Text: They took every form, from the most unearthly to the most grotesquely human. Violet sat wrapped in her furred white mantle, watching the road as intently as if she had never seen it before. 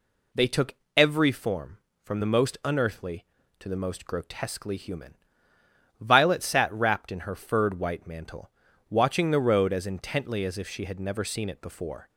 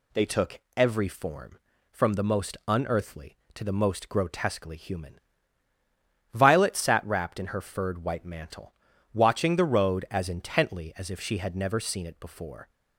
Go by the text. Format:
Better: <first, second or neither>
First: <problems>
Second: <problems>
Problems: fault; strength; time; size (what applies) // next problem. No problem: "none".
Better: neither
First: pauses between "took" and "every"; slight; at 0.7 s; 0.22 s long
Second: pauses between "took" and "every"; slight; at 0.5 s; 0.18 s long